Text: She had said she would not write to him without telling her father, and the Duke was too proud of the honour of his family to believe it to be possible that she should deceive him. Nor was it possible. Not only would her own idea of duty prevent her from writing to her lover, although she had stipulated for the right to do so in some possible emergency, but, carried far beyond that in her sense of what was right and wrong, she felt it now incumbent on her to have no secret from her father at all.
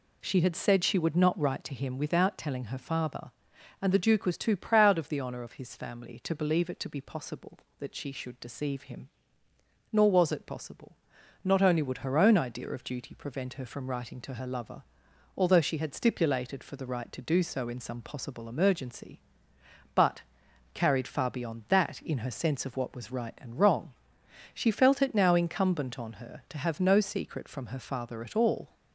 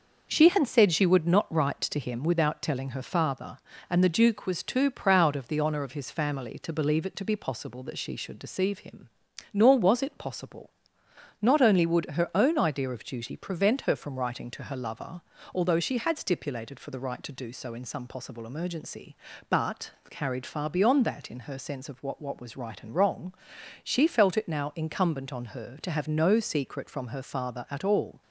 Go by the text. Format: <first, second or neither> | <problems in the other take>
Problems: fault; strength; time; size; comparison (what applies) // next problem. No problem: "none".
first | says "what" twice; at 22.2 s